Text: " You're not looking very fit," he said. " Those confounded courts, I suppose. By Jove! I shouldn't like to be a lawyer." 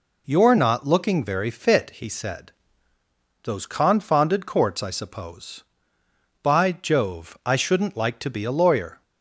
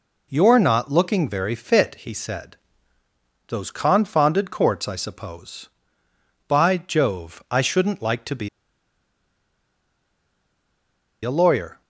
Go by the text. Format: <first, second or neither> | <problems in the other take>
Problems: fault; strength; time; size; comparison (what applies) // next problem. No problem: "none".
first | pauses between "be" and "a"; strong; at 8.4 s; 2.7 s long